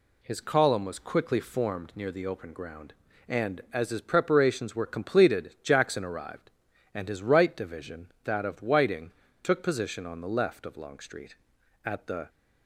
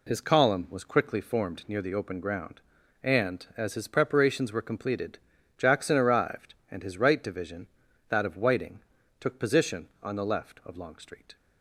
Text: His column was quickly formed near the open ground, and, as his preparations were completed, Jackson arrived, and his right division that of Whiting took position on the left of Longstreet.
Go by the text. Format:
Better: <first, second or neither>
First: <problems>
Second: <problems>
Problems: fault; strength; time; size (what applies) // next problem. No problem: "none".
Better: second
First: pauses between "Whiting" and "took"; slight; at 9.1 s; 0.32 s long // goes on to say "At the"; slight; from 11.8 s on; 0.44 s long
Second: pauses between "Whiting" and "took"; at 8.7 s; 0.40 s long